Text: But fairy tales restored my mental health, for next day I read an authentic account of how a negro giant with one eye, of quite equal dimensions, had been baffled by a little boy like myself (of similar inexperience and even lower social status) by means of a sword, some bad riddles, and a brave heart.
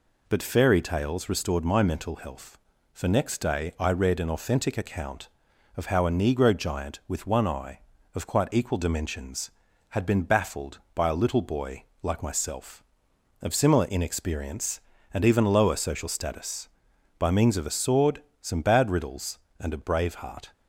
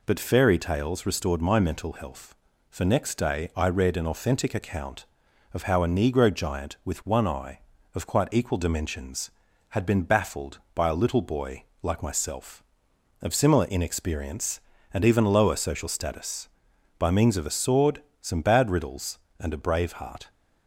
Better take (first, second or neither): neither